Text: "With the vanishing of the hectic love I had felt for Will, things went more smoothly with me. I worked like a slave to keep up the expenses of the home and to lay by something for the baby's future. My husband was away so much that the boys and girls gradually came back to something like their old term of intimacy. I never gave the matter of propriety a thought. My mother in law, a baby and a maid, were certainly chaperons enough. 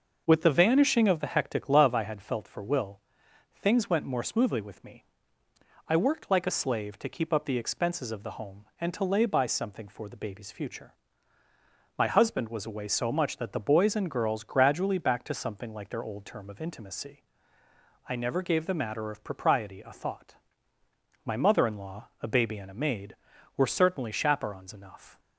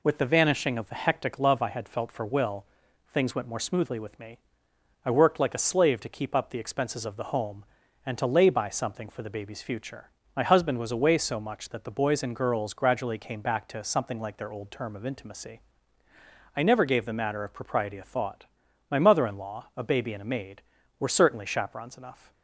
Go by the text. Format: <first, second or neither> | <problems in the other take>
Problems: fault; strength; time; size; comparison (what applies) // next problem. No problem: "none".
second | starts louder than the rest; noticeable; until 1.2 s; 6 dB // skips "came"; at 14.9 s